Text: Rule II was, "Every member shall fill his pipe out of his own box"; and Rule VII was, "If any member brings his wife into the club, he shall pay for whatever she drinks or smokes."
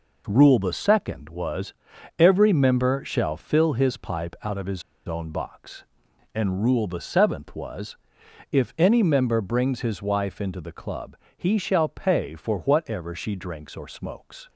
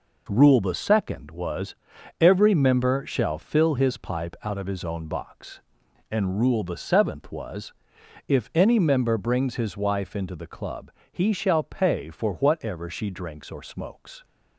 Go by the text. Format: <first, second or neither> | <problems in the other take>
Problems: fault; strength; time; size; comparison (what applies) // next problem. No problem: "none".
second | pauses between "his" and "own"; slight; at 4.8 s; 0.25 s long